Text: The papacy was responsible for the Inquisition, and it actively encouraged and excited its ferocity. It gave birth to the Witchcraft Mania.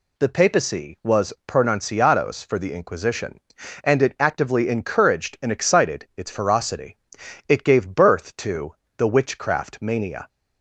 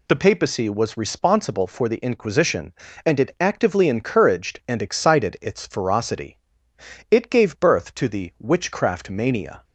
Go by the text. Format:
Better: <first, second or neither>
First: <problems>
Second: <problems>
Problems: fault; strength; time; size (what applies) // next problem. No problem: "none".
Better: second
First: says "pronunciados" for "responsible"; at 1.4 s // pauses between "to" and "the"; slight; at 8.7 s; 0.24 s long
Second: none